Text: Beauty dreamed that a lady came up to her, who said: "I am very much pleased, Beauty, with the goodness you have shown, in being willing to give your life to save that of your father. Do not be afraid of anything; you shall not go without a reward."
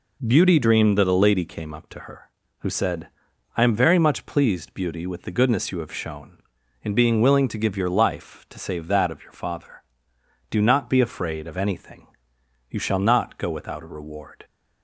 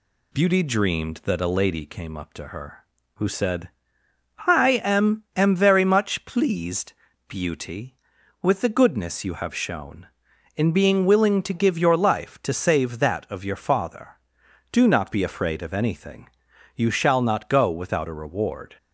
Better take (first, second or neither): first